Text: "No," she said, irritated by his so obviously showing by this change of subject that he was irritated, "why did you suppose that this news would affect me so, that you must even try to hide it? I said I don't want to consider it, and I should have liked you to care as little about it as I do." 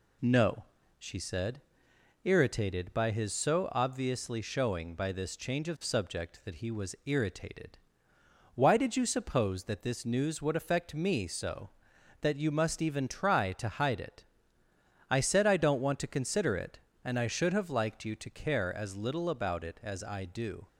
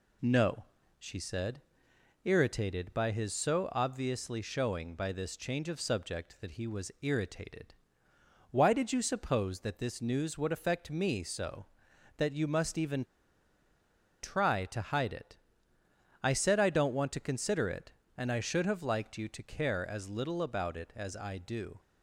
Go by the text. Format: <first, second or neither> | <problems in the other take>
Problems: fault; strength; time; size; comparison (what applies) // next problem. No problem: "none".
first | pauses between "even" and "try"; at 13.0 s; 1.1 s long